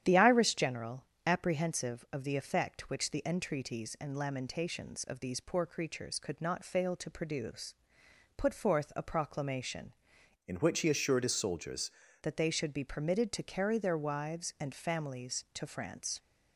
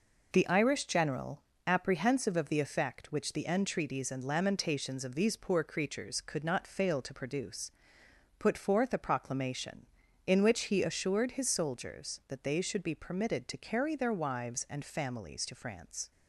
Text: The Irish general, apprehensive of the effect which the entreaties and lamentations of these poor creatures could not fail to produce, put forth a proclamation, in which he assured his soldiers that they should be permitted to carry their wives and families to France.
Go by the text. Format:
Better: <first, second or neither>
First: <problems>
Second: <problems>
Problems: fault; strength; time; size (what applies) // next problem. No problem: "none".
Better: second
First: starts louder than the rest; strong; until 1.0 s; 10 dB // changes voice from "in" to "soldiers"; from 10.4 to 11.8 s; 1.4 s long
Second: none